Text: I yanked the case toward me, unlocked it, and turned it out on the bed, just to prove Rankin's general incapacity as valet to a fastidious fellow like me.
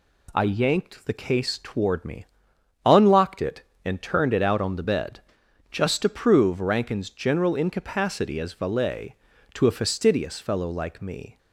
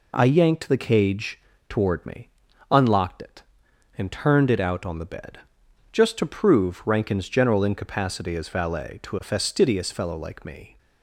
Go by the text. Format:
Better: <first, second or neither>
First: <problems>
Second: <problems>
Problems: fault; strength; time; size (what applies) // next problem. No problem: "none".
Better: first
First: none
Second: says "cage" for "case"; at 0.7 s